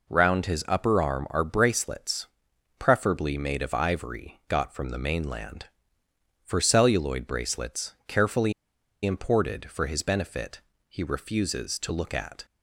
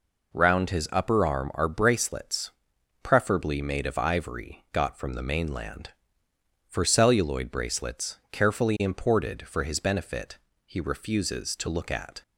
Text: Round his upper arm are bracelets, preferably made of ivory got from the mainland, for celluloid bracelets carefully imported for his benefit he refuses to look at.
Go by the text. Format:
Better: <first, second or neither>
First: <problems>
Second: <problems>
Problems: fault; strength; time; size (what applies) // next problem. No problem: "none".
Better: second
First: pauses between "carefully" and "imported"; noticeable; at 8.5 s; 0.52 s long // pauses between "benefit" and "he"; slight; at 10.6 s; 0.26 s long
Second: pauses between "benefit" and "he"; slight; at 10.3 s; 0.26 s long